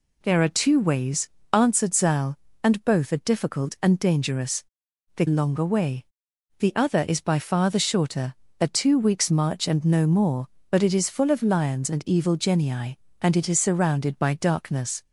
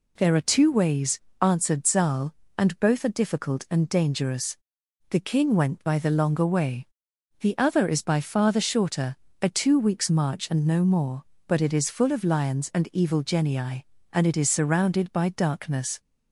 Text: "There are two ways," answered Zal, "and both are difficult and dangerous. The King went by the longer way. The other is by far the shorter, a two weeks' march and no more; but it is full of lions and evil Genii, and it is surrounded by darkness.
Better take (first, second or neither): second